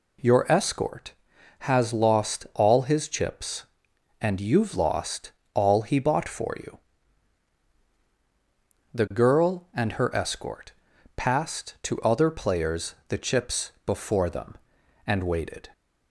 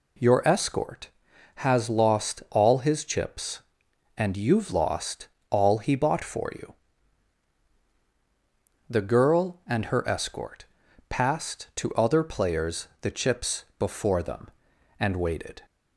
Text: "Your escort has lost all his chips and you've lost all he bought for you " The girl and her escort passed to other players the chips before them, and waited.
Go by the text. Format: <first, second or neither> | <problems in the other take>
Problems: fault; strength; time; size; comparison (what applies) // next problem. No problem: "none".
neither | pauses between "lost" and "all"; slight; the same in both // pauses between "escort" and "passed"; noticeable; the same in both